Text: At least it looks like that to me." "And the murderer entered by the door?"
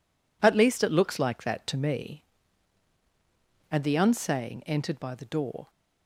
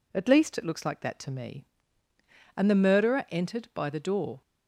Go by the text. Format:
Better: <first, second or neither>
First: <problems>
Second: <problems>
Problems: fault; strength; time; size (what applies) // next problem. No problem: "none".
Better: second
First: says "unsaying" for "murderer"; at 3.9 s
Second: none